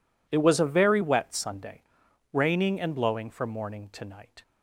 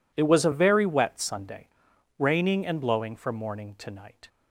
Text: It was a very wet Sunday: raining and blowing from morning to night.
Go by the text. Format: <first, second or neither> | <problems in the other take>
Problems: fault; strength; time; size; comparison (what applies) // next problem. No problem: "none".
neither | none